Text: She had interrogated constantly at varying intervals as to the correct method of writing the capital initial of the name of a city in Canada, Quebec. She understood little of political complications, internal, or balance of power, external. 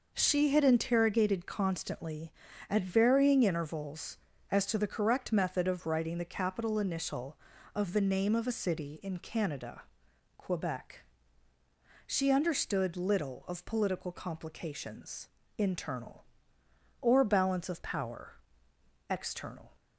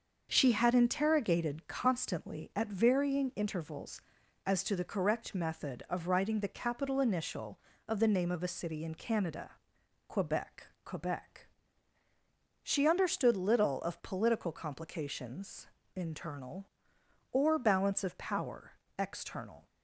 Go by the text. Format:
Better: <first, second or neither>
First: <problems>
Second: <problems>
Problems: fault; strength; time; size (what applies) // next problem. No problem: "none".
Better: first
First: none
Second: starts louder than the rest; until 1.3 s; 6.5 dB // says "Quebec" twice; at 10.8 s